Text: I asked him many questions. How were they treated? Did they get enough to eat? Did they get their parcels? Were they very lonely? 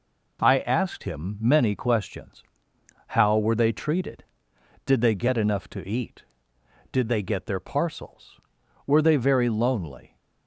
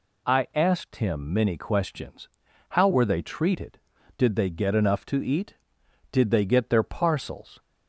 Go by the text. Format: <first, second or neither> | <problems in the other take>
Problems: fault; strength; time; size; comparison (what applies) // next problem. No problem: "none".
first | stops before "Were they very lonely"; at 7.5 s